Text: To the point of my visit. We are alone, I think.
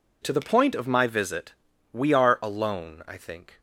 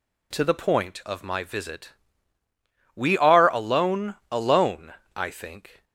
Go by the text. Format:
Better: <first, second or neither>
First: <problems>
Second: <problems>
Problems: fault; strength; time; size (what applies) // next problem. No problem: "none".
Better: first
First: none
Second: says "alone" twice; at 4.3 s